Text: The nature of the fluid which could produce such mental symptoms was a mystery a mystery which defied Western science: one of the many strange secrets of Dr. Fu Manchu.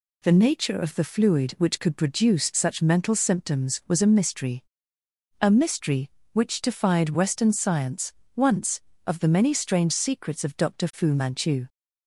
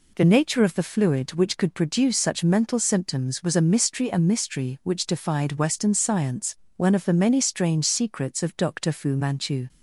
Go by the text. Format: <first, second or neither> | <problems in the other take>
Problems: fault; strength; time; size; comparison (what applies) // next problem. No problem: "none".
second | pauses between "mystery" and "a"; noticeable; at 4.6 s; 0.76 s long // says "once" for "one"; at 8.3 s